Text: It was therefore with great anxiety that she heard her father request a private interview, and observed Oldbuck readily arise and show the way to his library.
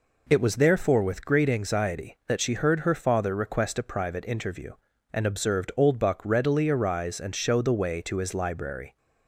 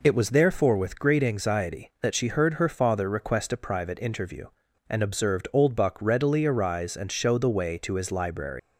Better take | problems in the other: first | leaves "library" unfinished; at 8.5 s; 145 ms

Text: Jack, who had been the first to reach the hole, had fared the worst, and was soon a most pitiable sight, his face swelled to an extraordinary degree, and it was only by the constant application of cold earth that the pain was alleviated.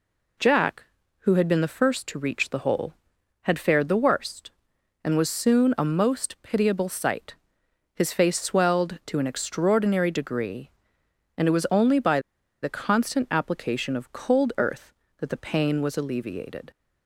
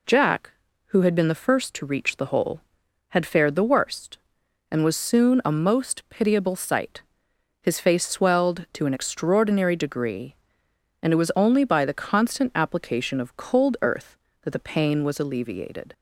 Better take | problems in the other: second | pauses between "by" and "the"; at 12.1 s; 0.43 s long

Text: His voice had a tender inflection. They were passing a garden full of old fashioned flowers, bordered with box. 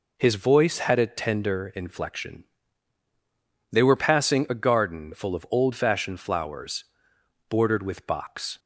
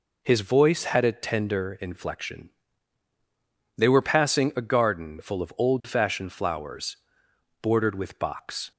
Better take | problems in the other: neither | none

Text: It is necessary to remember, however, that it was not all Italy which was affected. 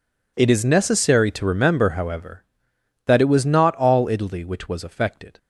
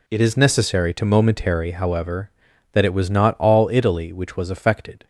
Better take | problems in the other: first | says "momentary" for "remember"; at 1.0 s

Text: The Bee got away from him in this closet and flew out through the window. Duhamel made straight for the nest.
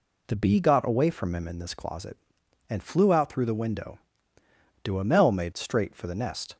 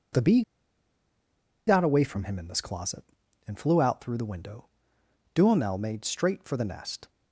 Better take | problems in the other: first | pauses between "Bee" and "got"; strong; at 0.4 s; 1.2 s long

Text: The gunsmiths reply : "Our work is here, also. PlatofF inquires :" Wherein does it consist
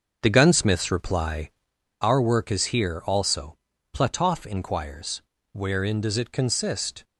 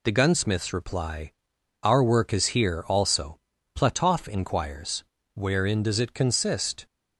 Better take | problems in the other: second | starts louder than the rest; until 1.7 s; 7 dB

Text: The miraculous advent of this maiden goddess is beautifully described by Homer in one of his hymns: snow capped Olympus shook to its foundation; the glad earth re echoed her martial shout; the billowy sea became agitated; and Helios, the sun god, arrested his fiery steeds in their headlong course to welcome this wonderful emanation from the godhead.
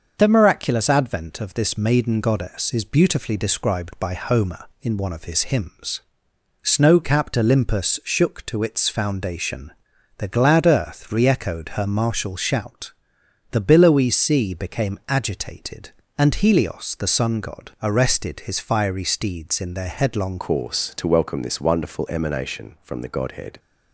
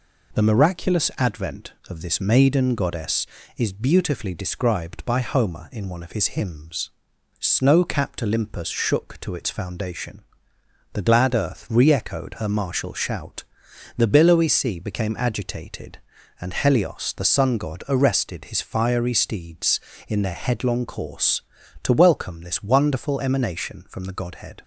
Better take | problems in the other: second | starts louder than the rest; until 1.1 s; 6.5 dB // changes voice at "course"; from 20.3 s on; 3.2 s long

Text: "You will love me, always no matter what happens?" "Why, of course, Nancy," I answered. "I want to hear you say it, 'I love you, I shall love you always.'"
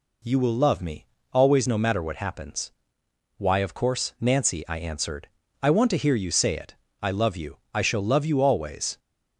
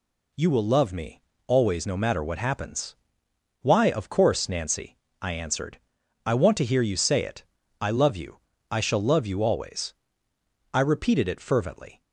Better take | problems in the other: first | goes on to say "I repeated it fervently"; noticeable; from 10.7 s on; 1.3 s long

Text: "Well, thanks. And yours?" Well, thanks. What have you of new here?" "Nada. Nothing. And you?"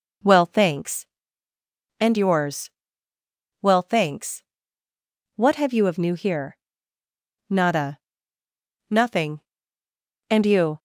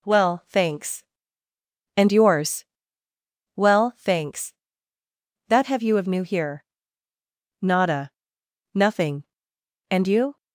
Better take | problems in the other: first | says "That" for "What"; at 5.4 s

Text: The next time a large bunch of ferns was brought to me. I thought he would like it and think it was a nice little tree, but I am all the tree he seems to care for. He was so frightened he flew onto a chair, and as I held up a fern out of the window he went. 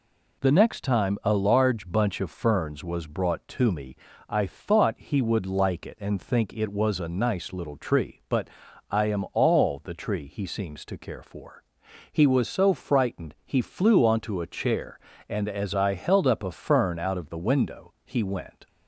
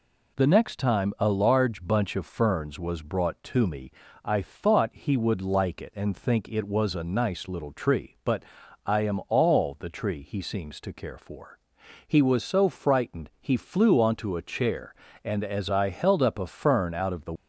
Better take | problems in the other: first | pauses between "but" and "I"; at 8.4 s; 0.44 s long; also in the first // stops before "window he went"; at 17.3 s

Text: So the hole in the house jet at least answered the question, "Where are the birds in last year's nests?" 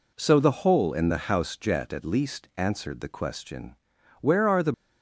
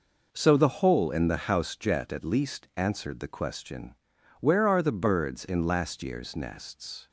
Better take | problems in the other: second | stops before "birds in last year's nests"; at 4.7 s

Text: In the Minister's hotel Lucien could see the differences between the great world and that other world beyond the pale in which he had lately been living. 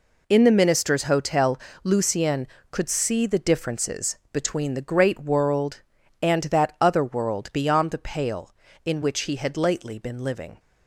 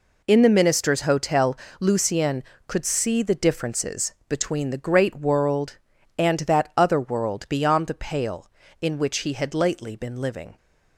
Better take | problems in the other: neither | pauses between "hotel" and "Lucien"; slight; the same in both // pauses between "differences" and "between"; slight; the same in both

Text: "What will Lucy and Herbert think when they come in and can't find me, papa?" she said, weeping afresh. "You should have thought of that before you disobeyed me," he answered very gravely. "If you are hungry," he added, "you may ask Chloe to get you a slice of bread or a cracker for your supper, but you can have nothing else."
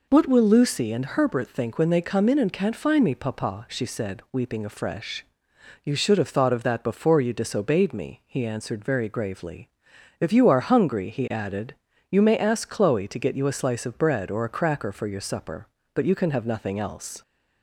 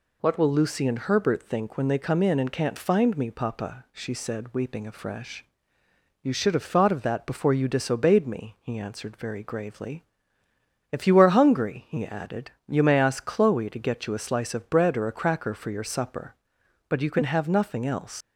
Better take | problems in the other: first | leaves "else" unfinished; at 18.2 s; 100 ms

